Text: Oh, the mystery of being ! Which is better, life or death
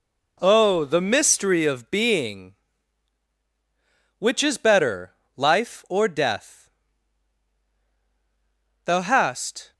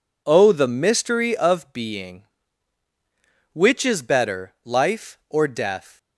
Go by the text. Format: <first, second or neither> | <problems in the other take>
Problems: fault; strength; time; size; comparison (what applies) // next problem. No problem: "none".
second | goes on to say "Thou hast"; noticeable; from 8.8 s on; 0.88 s long